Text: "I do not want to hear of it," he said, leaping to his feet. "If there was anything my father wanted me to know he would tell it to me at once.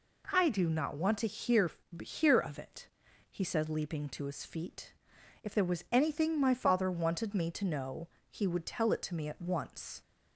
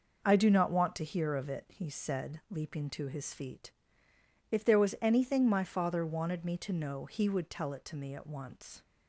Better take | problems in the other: second | says "hear" twice; at 2.0 s // pauses between "know" and "he"; slight; at 8.0 s; 0.20 s long

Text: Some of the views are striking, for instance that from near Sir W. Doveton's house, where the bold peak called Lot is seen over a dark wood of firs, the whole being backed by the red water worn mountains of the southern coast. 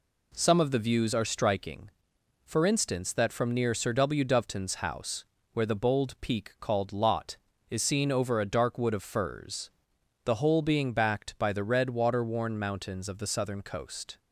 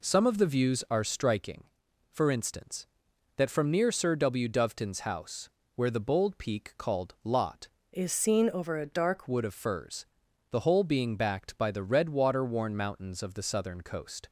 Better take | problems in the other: first | changes voice from "is" to "dark"; from 7.9 to 9.2 s; 1.3 s long

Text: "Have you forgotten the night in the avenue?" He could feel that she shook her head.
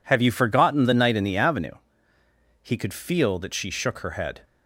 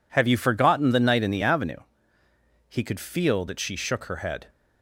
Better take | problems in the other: neither | none

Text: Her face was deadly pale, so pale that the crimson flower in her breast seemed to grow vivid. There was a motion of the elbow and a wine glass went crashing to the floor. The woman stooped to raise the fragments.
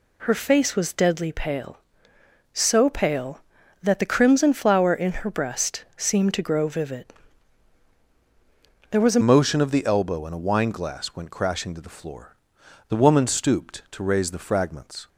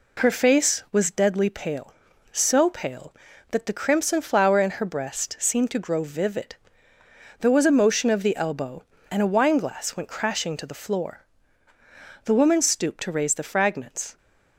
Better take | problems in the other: second | changes voice at "motion"; from 9.2 s on; 5.8 s long

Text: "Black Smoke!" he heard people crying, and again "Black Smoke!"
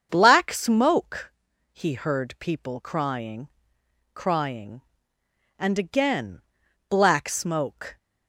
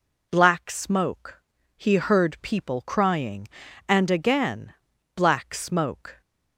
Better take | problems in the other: second | starts louder than the rest; until 1.1 s; 7 dB // says "crying" twice; at 4.1 s // pauses between "again" and "Black"; noticeable; at 6.4 s; 0.46 s long; also in the second

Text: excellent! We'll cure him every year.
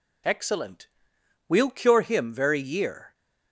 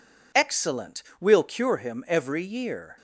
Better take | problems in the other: second | says "very" for "every"; at 2.3 s

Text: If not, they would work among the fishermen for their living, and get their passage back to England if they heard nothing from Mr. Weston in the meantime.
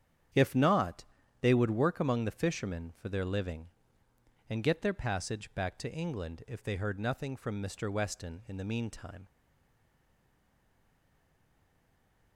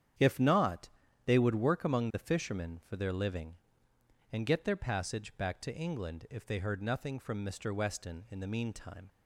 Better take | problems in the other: second | starts louder than the rest; strong; until 1.7 s; 9 dB; strong in the second // stays silent after the last word; strong; from 9.2 s on; 3.1 s long

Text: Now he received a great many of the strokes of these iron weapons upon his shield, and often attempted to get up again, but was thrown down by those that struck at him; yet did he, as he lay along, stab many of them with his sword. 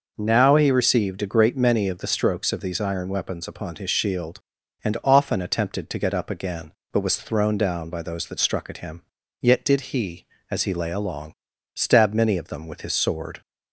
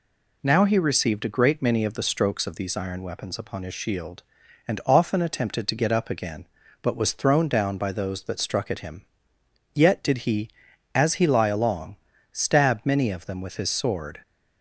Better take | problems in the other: first | says "lie" for "lay"; at 11.2 s

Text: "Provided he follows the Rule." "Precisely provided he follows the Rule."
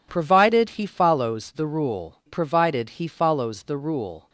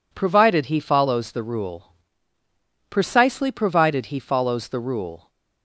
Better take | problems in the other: second | skips "Precisely"; at 2.2 s

